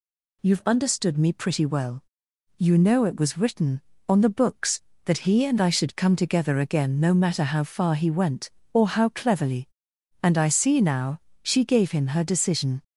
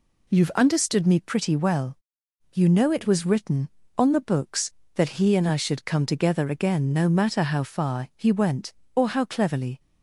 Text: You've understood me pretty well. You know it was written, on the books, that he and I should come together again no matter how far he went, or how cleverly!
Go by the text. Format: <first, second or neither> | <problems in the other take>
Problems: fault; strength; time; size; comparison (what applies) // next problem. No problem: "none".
second | goes on to say "And I see now she gave him her decision"; strong; from 10.2 s on; 2.6 s long